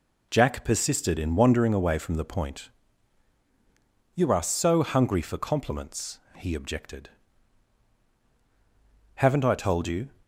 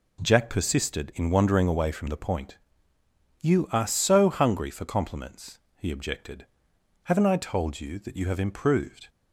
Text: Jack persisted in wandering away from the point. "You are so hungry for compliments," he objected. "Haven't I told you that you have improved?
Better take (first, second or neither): second